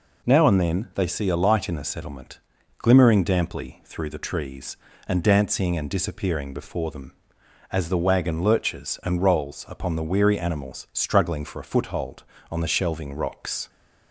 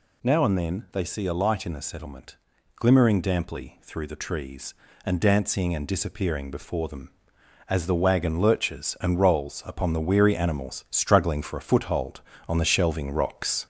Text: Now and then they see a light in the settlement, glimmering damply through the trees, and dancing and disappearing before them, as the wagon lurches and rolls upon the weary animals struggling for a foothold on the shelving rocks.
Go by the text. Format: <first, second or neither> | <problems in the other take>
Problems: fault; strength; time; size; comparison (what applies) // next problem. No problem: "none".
first | gets louder; throughout; 3.5 dB